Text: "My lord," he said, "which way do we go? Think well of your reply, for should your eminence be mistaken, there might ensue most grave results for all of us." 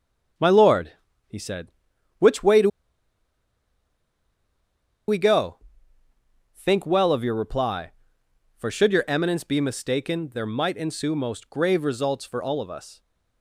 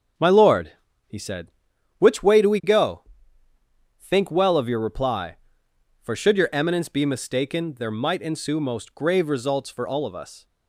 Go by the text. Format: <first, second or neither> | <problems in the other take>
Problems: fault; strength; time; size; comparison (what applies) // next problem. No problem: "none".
second | starts louder than the rest; until 2.2 s; 6.5 dB; also in the second // pauses between "do" and "we"; strong; at 2.6 s; 2.4 s long